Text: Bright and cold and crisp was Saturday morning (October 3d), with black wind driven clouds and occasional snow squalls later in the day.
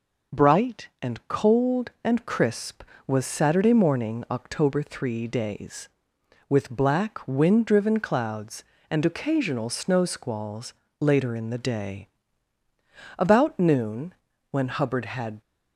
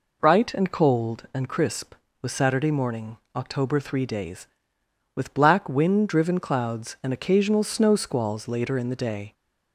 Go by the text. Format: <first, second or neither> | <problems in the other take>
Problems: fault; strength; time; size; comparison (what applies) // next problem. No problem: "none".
second | pauses between "squalls" and "later"; slight; at 10.7 s; 0.28 s long // goes on to say "About noon when Hubbard had"; strong; from 13.1 s on; 2.2 s long